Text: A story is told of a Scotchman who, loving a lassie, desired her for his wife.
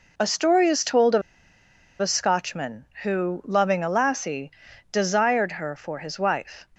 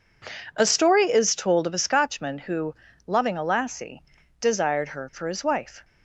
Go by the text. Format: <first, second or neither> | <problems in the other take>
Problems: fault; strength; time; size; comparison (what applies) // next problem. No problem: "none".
second | pauses between "of" and "a"; noticeable; at 1.2 s; 0.79 s long